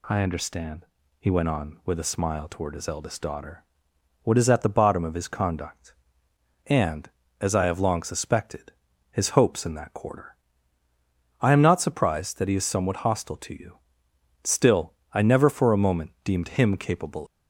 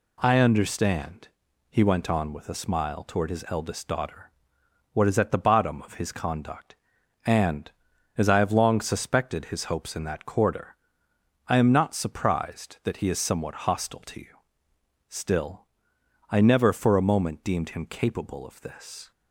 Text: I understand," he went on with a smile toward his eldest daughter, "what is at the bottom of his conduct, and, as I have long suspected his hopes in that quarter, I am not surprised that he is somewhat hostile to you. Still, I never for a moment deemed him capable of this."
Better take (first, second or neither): second